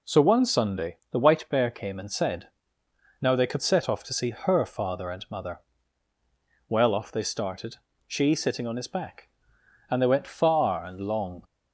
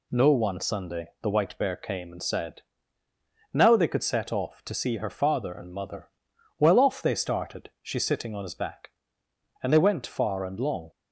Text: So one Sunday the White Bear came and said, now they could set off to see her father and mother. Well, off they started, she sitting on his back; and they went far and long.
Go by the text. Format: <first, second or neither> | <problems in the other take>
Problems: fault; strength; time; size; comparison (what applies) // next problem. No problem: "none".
first | says "No" for "So"; at 0.1 s